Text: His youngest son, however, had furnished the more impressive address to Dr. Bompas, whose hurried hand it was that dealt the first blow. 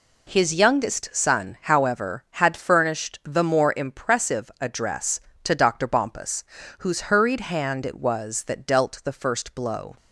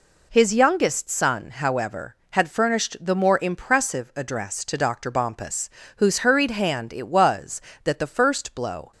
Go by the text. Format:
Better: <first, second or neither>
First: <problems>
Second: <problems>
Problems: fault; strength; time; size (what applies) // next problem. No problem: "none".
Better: first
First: none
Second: skips "dealt"; at 7.9 s